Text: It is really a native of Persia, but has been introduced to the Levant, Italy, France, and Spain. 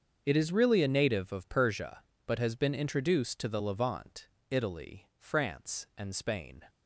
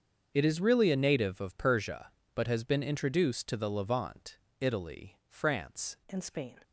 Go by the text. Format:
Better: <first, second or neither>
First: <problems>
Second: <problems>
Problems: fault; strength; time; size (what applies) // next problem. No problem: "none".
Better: first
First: starts louder than the rest; until 1.2 s; 6.5 dB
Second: starts louder than the rest; until 1.3 s; 6.5 dB // changes voice at "and"; from 6.1 s on; 0.4 s long